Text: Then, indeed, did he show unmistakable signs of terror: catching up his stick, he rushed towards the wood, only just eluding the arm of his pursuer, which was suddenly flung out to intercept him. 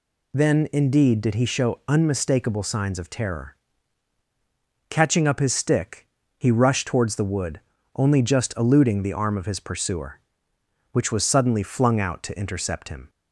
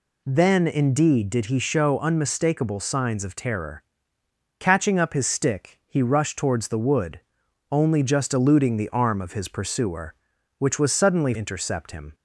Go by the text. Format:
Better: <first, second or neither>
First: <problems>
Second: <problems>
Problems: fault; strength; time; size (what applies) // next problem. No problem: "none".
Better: first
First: none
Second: skips "flung out to"; at 11.3 s